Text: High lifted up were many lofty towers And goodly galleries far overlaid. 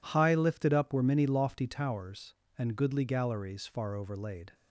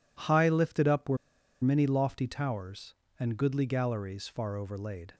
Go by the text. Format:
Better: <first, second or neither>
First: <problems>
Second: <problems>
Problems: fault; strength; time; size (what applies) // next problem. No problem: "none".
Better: first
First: none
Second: pauses between "were" and "many"; noticeable; at 1.1 s; 0.47 s long